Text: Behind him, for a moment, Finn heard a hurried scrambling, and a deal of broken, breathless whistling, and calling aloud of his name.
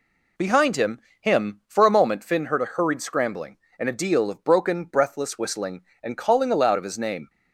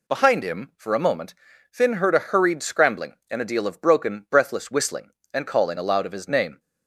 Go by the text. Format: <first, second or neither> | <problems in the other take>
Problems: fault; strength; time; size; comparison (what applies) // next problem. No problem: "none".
second | says "him" twice; at 1.2 s